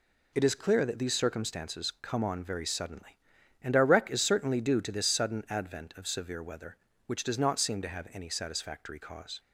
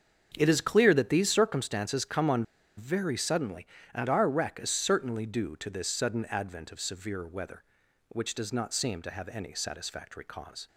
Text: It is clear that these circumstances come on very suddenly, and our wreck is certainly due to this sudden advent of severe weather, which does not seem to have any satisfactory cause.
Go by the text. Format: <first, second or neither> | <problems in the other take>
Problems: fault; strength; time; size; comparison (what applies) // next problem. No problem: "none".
first | starts louder than the rest; strong; until 1.3 s; 7 dB // pauses between "on" and "very"; slight; at 2.4 s; 0.34 s long